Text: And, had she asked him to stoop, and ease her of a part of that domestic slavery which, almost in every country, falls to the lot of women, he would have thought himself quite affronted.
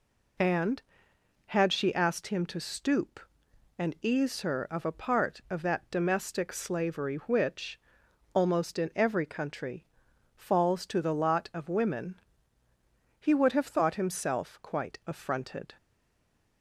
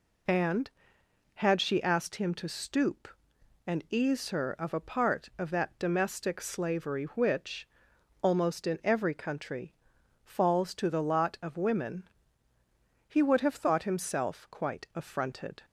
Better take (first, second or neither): second